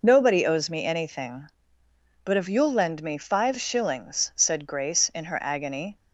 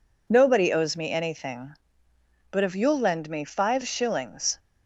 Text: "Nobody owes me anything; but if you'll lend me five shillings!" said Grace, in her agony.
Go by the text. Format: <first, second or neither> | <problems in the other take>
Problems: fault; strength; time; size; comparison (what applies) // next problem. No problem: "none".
first | stops before "said Grace in her agony"; at 4.5 s